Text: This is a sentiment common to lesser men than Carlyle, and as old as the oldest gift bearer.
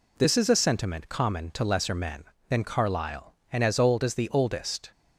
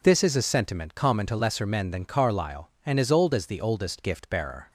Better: second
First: stops before "gift bearer"; at 4.9 s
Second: none

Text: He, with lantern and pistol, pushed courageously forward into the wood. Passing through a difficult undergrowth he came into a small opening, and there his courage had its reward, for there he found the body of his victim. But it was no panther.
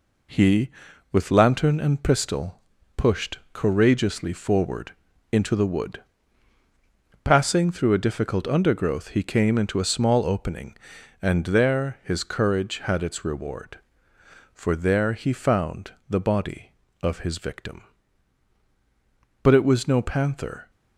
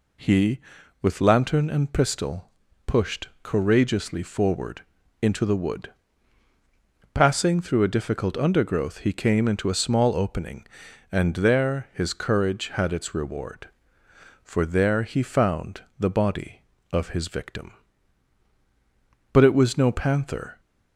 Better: second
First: gets quieter; noticeable; throughout; 5 dB // pauses between "forward" and "into"; at 4.9 s; 0.40 s long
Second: pauses between "forward" and "into"; at 4.8 s; 0.40 s long

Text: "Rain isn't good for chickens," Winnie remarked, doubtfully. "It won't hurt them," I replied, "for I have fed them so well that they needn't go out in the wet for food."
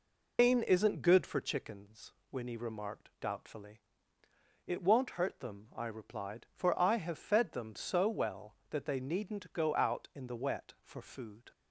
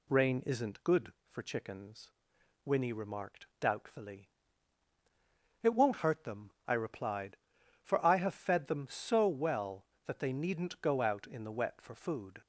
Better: second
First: loses the start of "Rain"; at 0.3 s; 175 ms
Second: none

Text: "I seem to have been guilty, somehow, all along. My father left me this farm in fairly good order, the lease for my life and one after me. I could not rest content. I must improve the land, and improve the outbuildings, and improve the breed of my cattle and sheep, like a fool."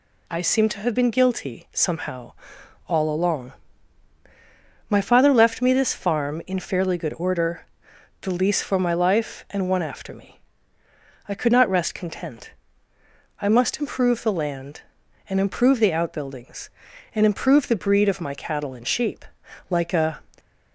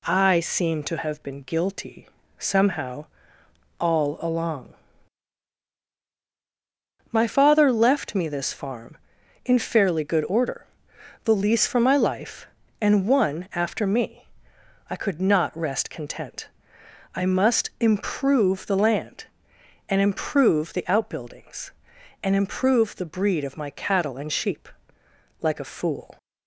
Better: second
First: stops before "fool"; at 20.3 s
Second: none

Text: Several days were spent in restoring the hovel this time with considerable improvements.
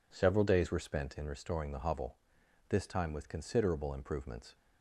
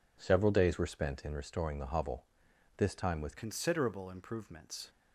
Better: first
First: pauses between "hovel" and "this"; noticeable; at 2.1 s; 0.50 s long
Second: pauses between "hovel" and "this"; noticeable; at 2.2 s; 0.50 s long // changes voice at "considerable"; from 3.3 s on; 1.5 s long

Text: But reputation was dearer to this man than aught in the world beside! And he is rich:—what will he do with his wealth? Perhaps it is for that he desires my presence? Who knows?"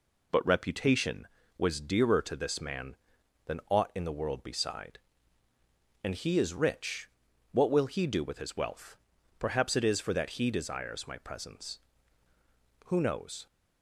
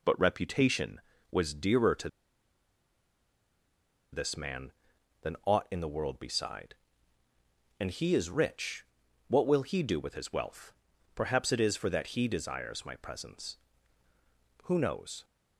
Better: first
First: none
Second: pauses between "to" and "this"; strong; at 2.0 s; 2.0 s long

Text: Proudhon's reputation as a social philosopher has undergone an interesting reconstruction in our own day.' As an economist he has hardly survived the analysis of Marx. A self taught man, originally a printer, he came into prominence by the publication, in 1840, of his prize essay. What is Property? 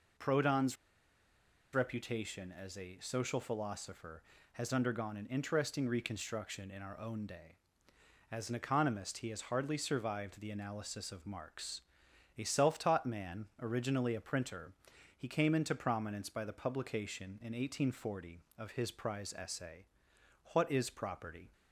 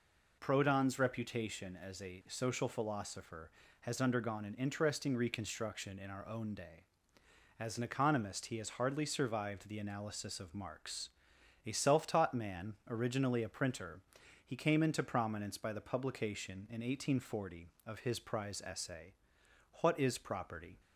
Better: second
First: pauses between "Proudhon's" and "reputation"; noticeable; at 0.7 s; 0.98 s long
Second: none

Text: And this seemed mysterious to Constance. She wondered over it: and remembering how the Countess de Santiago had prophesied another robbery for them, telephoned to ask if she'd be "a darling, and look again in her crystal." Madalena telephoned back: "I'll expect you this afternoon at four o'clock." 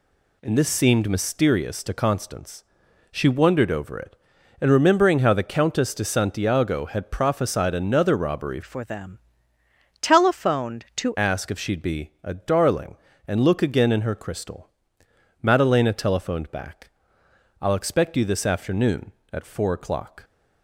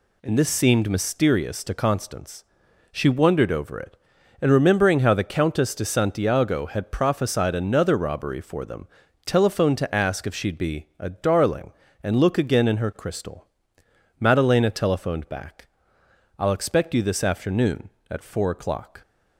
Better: second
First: changes voice from "for" to "to"; from 8.6 to 11.1 s; 2.5 s long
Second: none

